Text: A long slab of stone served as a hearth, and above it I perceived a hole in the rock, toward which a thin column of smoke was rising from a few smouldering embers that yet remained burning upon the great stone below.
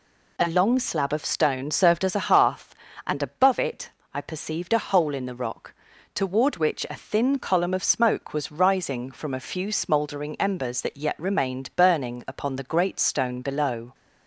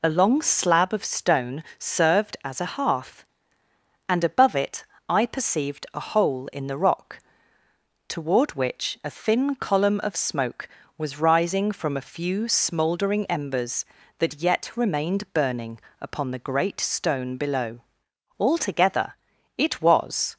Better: first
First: pauses between "it" and "I"; slight; at 3.9 s; 0.24 s long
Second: pauses between "it" and "I"; slight; at 4.8 s; 0.23 s long // pauses between "burning" and "upon"; slight; at 15.8 s; 0.20 s long // goes on to say "Altogether it was"; strong; from 18.3 s on; 1.9 s long

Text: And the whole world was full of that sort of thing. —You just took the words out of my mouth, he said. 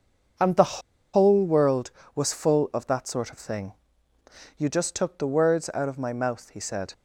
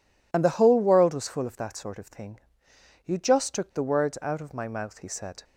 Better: second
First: starts louder than the rest; until 1.7 s; 6.5 dB // pauses between "the" and "whole"; slight; at 0.8 s; 0.33 s long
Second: none

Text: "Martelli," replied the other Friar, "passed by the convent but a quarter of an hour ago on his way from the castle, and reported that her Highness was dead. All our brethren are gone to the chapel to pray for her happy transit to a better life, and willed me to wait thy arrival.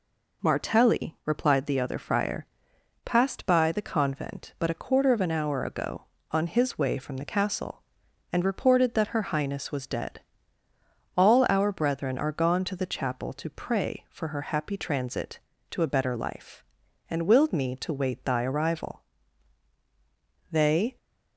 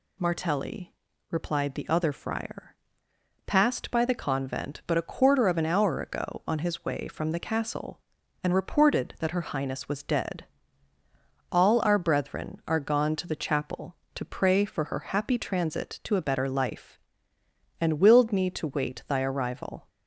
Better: second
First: goes on to say "They"; slight; from 20.5 s on; 0.46 s long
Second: none

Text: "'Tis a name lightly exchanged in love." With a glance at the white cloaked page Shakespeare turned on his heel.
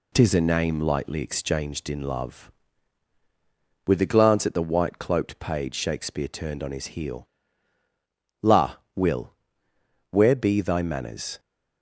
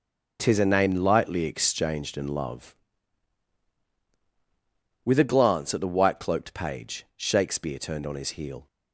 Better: second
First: goes on to say "La Will where be thy manners"; strong; from 8.4 s on; 2.9 s long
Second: none

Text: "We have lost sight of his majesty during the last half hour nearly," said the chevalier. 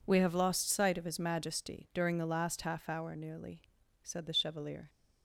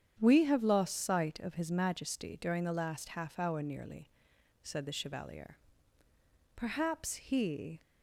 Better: first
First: none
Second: starts louder than the rest; strong; until 1.2 s; 8.5 dB // goes on to say "Perhaps he"; noticeable; from 6.5 s on; 1.2 s long

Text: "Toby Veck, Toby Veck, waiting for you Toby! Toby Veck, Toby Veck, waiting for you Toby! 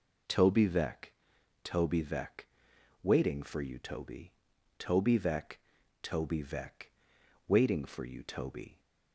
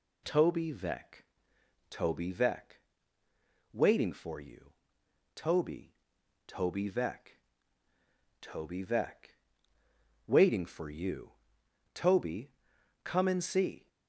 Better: first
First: none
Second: pauses between "you" and "Toby"; noticeable; at 4.7 s; 0.62 s long // pauses between "you" and "Toby"; noticeable; at 11.3 s; 0.60 s long // goes on to say "Come and see"; noticeable; from 13.0 s on; 0.84 s long

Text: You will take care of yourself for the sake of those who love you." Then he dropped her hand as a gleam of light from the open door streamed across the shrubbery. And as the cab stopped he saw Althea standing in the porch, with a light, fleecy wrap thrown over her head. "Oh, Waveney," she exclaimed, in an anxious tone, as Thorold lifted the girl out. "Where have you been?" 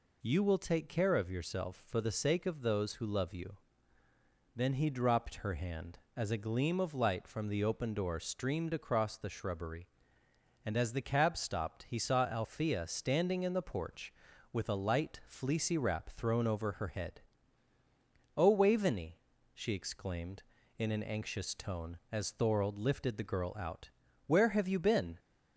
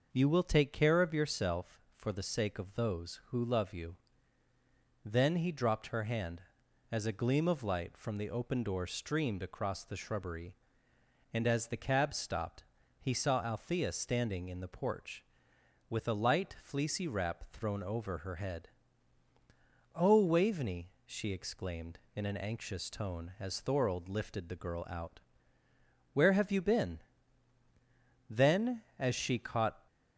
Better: first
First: none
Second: pauses between "stopped" and "he"; slight; at 12.6 s; 0.36 s long // goes on to say "Then as she caught"; from 28.2 s on; 1.5 s long

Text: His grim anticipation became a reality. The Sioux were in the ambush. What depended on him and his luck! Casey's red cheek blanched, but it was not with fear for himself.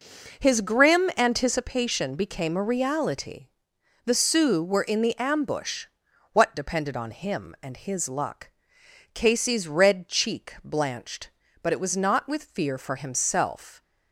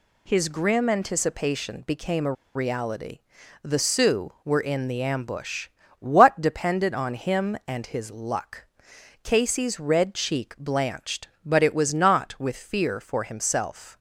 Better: first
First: none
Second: pauses between "a" and "reality"; slight; at 2.3 s; 0.22 s long

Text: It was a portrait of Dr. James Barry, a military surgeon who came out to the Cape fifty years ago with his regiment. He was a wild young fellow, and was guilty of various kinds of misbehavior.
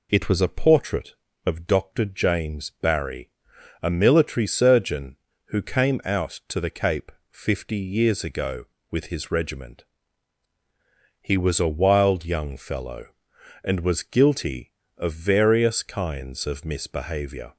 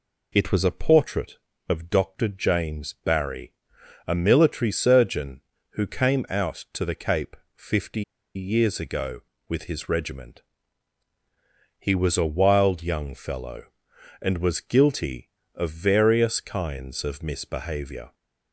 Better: first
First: pauses between "Cape" and "fifty"; slight; at 7.1 s; 0.20 s long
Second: pauses between "Cape" and "fifty"; slight; at 7.3 s; 0.20 s long // pauses between "fifty" and "years"; slight; at 8.0 s; 0.33 s long

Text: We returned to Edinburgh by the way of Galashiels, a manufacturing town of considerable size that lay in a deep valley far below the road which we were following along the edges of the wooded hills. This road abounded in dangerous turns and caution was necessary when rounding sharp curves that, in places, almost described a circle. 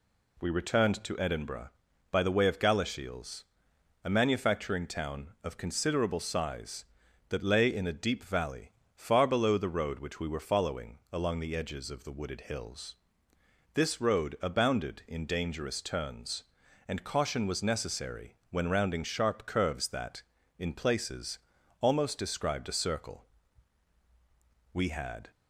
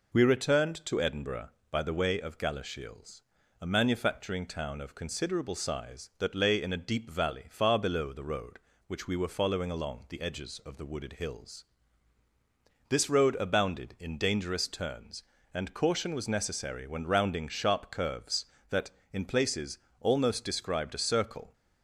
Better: second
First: pauses between "valley" and "far"; slight; at 8.6 s; 0.24 s long // goes on to say "We had"; from 24.7 s on; 0.56 s long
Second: none

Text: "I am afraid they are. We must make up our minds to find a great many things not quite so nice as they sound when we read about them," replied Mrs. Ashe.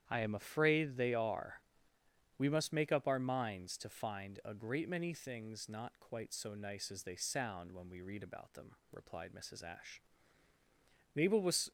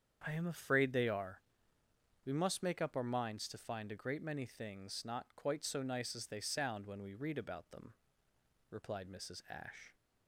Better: second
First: starts louder than the rest; strong; until 1.0 s; 9.5 dB // goes on to say "Mabel was"; from 11.1 s on; 0.56 s long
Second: starts louder than the rest; strong; until 1.2 s; 7.5 dB

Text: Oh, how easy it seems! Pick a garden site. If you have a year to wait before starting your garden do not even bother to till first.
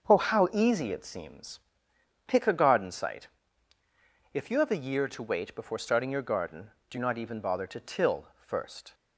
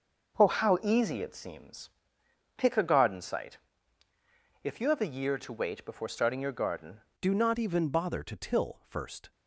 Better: first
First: starts louder than the rest; until 1.1 s; 7 dB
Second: starts louder than the rest; noticeable; until 1.4 s; 6 dB // changes voice at "do"; from 7.2 s on; 2.1 s long

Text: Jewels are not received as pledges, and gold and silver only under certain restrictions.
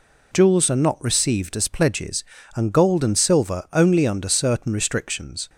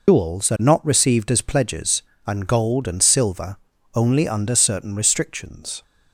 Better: first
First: none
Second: loses the start of "Jewels"; at 0.0 s; 130 ms // pauses between "silver" and "only"; slight; at 3.5 s; 0.34 s long

